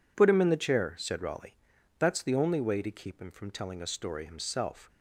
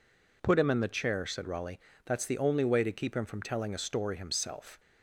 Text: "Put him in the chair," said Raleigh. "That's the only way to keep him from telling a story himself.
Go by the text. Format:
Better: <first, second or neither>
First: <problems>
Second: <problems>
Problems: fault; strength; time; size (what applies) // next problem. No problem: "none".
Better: neither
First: none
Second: none